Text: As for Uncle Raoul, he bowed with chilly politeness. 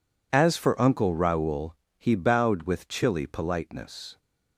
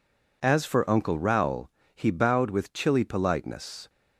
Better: neither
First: none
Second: none

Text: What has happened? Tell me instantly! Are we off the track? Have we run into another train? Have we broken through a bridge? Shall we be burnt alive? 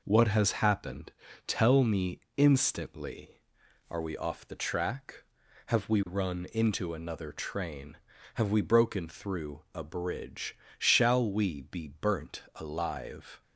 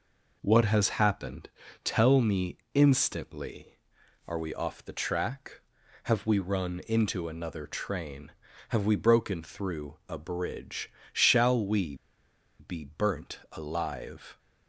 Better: first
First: pauses between "me" and "instantly"; slight; at 2.1 s; 0.18 s long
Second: pauses between "me" and "instantly"; slight; at 2.5 s; 0.18 s long // pauses between "we" and "be"; noticeable; at 11.9 s; 0.63 s long

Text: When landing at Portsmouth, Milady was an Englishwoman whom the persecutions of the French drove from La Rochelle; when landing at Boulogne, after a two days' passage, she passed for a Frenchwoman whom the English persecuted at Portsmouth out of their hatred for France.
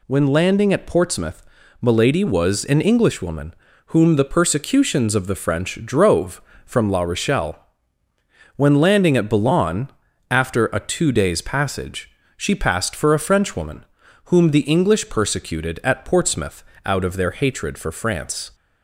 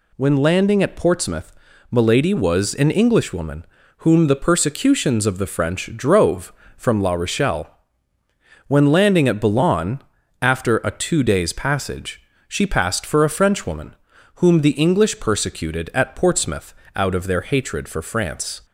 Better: neither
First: pauses between "Englishwoman" and "whom"; slight; at 3.5 s; 0.32 s long // pauses between "Frenchwoman" and "whom"; at 13.8 s; 0.40 s long // pauses between "Portsmouth" and "out"; slight; at 16.6 s; 0.20 s long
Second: pauses between "Englishwoman" and "whom"; slight; at 3.6 s; 0.32 s long // pauses between "Frenchwoman" and "whom"; at 13.9 s; 0.40 s long // pauses between "Portsmouth" and "out"; slight; at 16.7 s; 0.20 s long

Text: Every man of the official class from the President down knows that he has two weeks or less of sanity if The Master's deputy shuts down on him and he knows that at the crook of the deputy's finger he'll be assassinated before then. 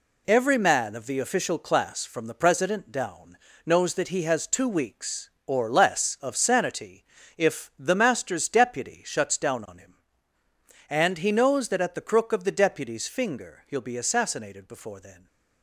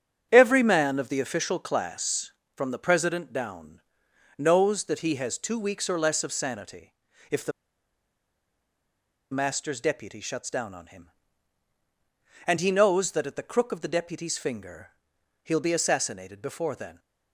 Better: first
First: pauses between "down" and "knows"; slight; at 3.3 s; 0.30 s long // pauses between "sanity" and "if"; slight; at 7.0 s; 0.32 s long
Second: starts louder than the rest; strong; until 1.3 s; 8.5 dB // pauses between "down" and "knows"; noticeable; at 3.8 s; 0.56 s long // pauses between "sanity" and "if"; at 6.9 s; 0.38 s long // pauses between "The" and "Master's"; strong; at 7.5 s; 1.8 s long // pauses between "finger" and "he'll"; noticeable; at 14.8 s; 0.54 s long

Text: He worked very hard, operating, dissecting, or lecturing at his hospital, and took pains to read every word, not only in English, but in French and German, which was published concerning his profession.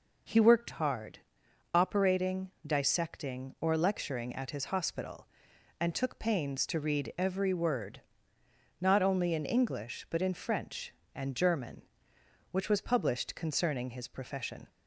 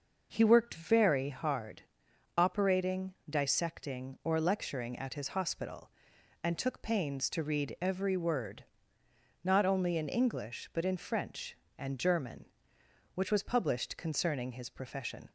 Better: second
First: skips "very"; at 0.7 s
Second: none

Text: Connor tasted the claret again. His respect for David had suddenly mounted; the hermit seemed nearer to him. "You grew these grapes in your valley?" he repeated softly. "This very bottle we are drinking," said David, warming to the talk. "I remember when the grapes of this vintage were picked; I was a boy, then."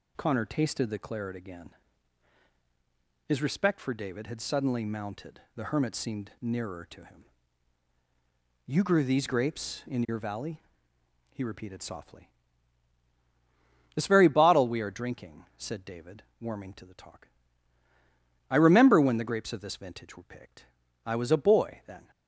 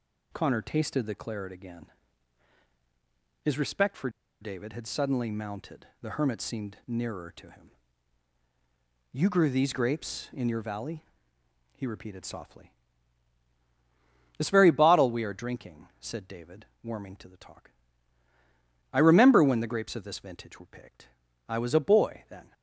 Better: first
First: none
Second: pauses between "for" and "David"; slight; at 4.0 s; 0.31 s long

